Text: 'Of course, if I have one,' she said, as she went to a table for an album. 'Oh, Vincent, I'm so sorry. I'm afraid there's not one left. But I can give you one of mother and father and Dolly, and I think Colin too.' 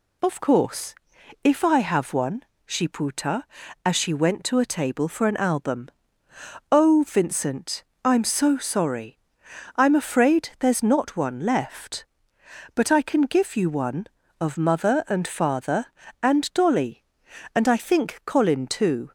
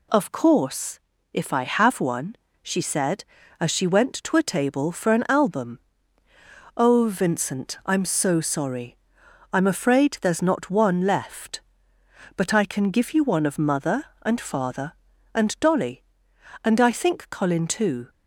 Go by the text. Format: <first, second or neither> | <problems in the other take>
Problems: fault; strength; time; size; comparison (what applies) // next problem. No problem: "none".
second | says "puta" for "said"; at 2.8 s